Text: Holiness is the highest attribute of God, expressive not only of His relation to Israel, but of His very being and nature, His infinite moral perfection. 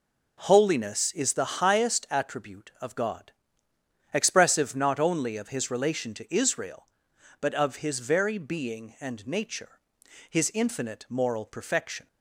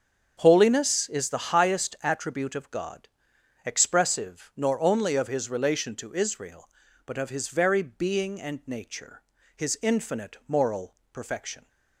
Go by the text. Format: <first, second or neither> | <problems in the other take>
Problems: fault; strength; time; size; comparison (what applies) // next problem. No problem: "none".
first | starts louder than the rest; until 1.3 s; 7 dB // says "nor" for "not"; at 4.5 s // pauses between "moral" and "perfection"; slight; at 10.9 s; 0.18 s long